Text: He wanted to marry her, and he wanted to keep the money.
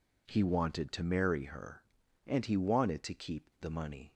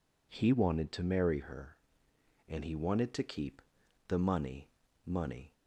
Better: first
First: none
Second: pauses between "keep" and "the"; noticeable; at 3.6 s; 0.46 s long // says "money" twice; at 5.0 s

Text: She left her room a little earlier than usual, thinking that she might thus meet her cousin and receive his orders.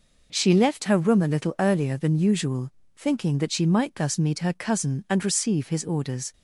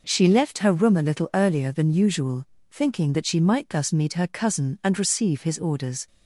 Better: neither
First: none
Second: none

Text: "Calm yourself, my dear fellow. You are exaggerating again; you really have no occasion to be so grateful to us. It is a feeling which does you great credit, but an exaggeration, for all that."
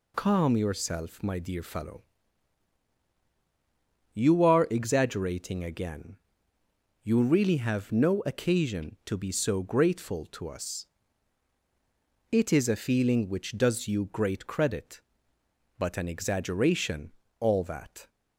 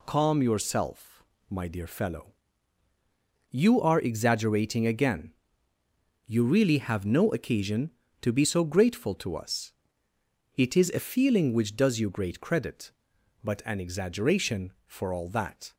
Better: second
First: skips "for"; at 17.2 s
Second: none

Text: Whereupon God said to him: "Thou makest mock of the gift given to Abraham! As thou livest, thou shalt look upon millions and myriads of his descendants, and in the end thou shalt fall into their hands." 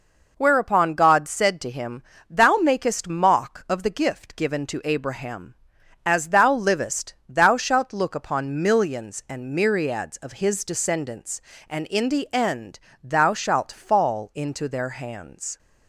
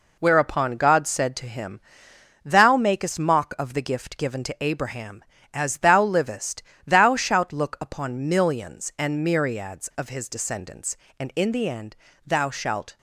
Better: first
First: pauses between "end" and "thou"; slight; at 12.7 s; 0.22 s long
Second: pauses between "end" and "thou"; slight; at 11.9 s; 0.28 s long // stops before "fall into their hands"; at 12.9 s

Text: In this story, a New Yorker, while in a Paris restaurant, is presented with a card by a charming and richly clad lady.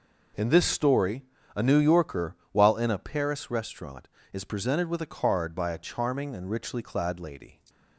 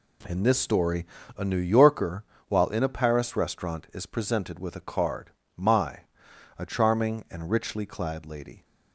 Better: first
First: none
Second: says "my" for "by"; at 5.5 s

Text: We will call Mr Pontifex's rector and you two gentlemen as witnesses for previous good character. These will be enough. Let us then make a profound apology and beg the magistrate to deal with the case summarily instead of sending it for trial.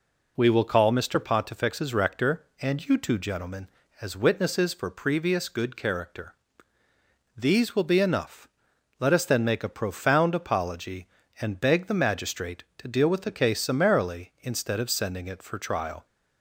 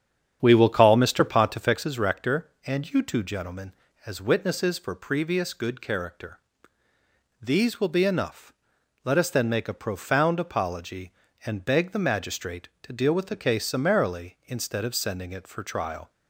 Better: first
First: none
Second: starts louder than the rest; strong; until 1.9 s; 8.5 dB

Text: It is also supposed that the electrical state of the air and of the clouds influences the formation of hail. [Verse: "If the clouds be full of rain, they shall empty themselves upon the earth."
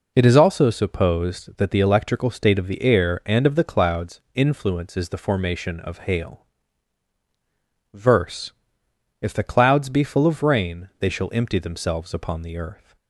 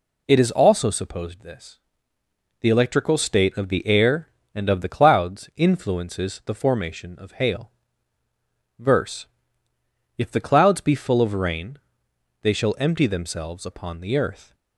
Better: first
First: none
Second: says "this" for "that"; at 1.4 s

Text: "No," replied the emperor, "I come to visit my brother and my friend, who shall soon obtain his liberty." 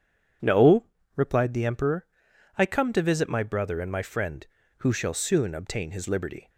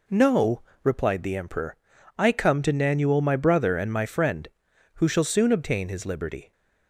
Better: first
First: none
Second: says "nanuel" for "visit"; at 2.7 s

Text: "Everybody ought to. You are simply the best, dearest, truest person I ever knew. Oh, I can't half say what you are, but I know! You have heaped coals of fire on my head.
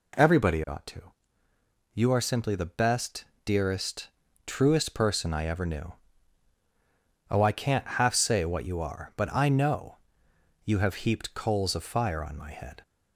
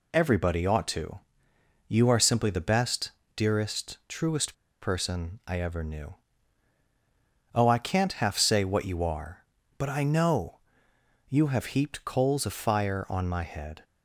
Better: first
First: none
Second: pauses between "truest" and "person"; slight; at 4.5 s; 0.26 s long

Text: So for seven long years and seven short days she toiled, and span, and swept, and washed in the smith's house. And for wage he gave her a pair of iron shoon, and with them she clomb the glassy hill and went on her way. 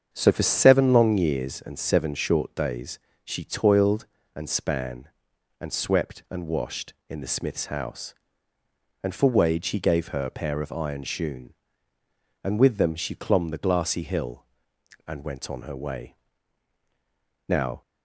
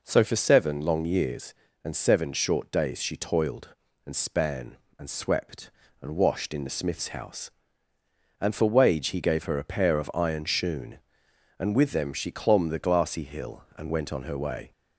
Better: second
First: starts louder than the rest; strong; until 1.1 s; 7.5 dB // pauses between "days" and "she"; slight; at 2.9 s; 0.24 s long // goes on to say "Now"; slight; from 17.4 s on; 0.34 s long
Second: none

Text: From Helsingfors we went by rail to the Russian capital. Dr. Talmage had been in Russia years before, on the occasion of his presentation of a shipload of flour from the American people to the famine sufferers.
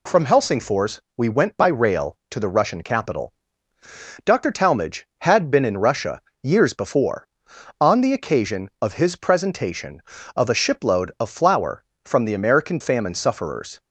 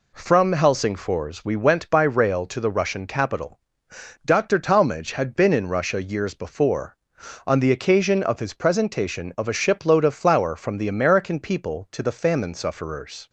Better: second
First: pauses between "Helsingfors" and "we"; slight; at 1.0 s; 0.16 s long // pauses between "Russia" and "years"; slight; at 6.2 s; 0.24 s long // skips "people to the"; at 12.7 s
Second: none

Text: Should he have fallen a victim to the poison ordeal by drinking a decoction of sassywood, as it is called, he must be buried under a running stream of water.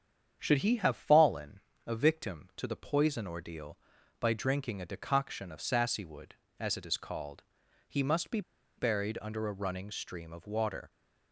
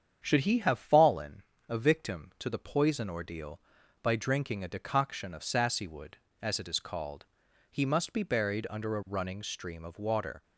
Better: second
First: starts louder than the rest; strong; until 1.4 s; 8 dB // pauses between "fallen" and "a"; slight; at 1.6 s; 0.24 s long // pauses between "be" and "buried"; at 8.4 s; 0.36 s long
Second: starts louder than the rest; strong; until 1.2 s; 8 dB // pauses between "fallen" and "a"; slight; at 1.4 s; 0.24 s long

